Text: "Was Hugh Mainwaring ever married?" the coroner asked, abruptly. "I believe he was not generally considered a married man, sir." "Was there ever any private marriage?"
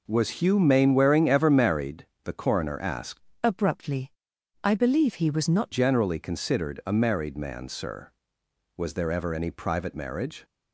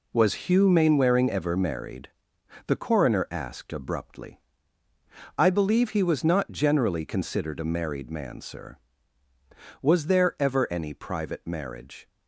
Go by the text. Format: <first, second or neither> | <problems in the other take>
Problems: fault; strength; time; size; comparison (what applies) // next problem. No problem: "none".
second | changes voice from "abruptly" to "not"; from 3.4 to 5.7 s; 2.3 s long